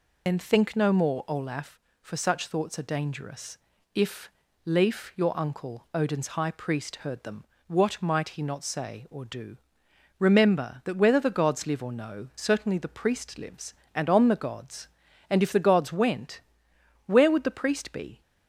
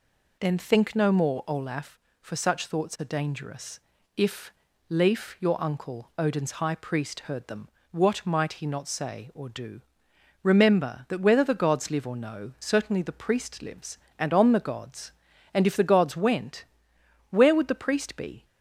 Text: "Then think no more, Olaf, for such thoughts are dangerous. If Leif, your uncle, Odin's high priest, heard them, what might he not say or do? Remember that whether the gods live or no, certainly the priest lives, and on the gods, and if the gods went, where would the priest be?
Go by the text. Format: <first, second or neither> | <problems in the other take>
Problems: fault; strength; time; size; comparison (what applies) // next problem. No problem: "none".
second | loses the start of "Then"; at 0.2 s; 55 ms // pauses between "If" and "Leif"; slight; at 4.3 s; 0.34 s long; slight in the second